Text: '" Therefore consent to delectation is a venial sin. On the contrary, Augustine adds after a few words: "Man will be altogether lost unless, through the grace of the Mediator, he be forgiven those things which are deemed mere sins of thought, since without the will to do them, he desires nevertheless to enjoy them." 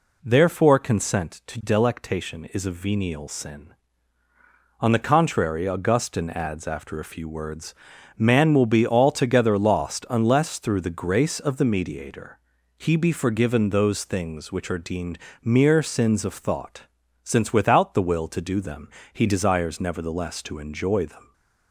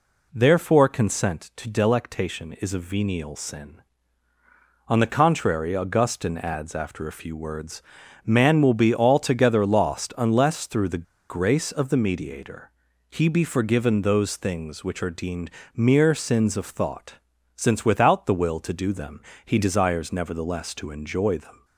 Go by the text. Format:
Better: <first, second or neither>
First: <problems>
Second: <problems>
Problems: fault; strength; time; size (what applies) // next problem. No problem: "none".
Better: first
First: pauses between "deemed" and "mere"; slight; at 15.1 s; 0.24 s long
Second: pauses between "the" and "grace"; slight; at 11.0 s; 0.27 s long // pauses between "deemed" and "mere"; slight; at 15.5 s; 0.24 s long